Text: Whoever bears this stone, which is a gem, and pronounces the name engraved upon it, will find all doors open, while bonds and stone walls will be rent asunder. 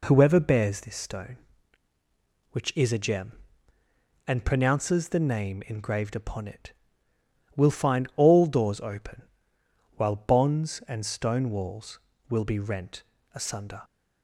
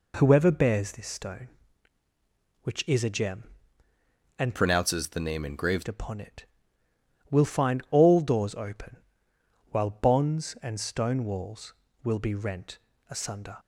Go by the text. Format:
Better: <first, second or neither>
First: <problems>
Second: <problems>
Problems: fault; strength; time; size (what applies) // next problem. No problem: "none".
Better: first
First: pauses between "rent" and "asunder"; slight; at 13.0 s; 0.32 s long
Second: changes voice from "pronounces" to "engraved"; from 4.5 to 5.8 s; 1.3 s long // pauses between "rent" and "asunder"; slight; at 12.7 s; 0.32 s long